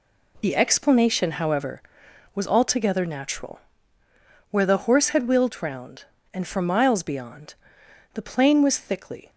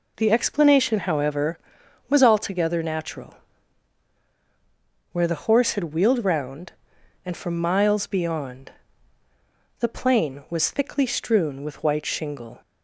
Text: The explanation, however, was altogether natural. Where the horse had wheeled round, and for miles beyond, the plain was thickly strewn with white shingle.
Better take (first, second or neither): second